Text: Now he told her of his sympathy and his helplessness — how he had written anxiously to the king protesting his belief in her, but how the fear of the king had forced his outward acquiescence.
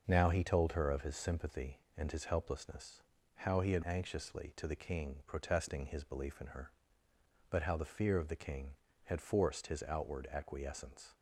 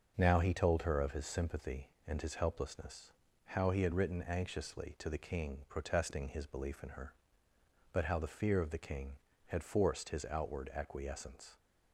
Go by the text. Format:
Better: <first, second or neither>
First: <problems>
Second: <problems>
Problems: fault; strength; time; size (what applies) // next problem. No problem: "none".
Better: second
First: starts louder than the rest; until 1.0 s; 6.5 dB // skips "written"; at 3.8 s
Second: starts louder than the rest; noticeable; until 1.1 s; 6 dB